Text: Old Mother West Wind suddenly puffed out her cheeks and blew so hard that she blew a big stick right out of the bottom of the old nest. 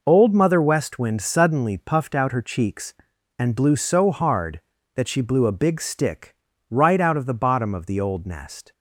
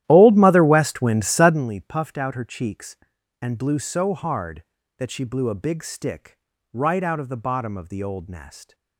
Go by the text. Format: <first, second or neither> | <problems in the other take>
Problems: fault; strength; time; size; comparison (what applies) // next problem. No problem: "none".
first | starts louder than the rest; strong; until 1.7 s; 13 dB // pauses between "stick" and "right"; at 6.3 s; 0.38 s long; also in the first